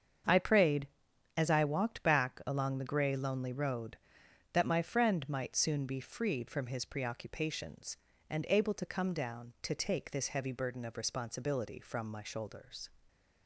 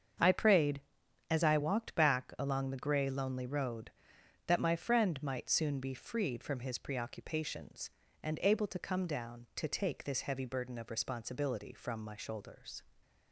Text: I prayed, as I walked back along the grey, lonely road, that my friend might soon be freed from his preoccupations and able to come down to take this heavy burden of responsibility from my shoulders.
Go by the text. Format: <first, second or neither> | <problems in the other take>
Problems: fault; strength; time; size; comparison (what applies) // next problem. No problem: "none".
neither | starts louder than the rest; strong; the same in both